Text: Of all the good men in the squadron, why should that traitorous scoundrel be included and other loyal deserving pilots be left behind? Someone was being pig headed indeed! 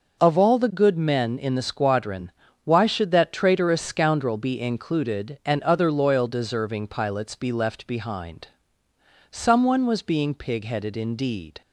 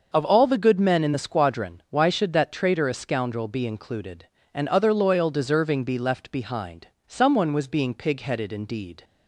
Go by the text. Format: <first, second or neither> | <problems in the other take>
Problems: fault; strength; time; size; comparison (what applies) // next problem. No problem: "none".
first | starts louder than the rest; until 1.1 s; 6 dB; noticeable in the first // skips "pilots"; at 5.8 s